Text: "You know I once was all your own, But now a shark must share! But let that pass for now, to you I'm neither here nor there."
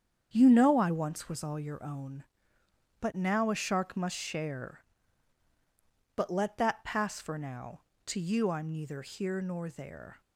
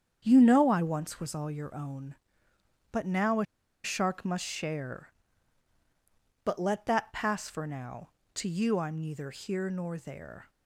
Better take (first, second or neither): first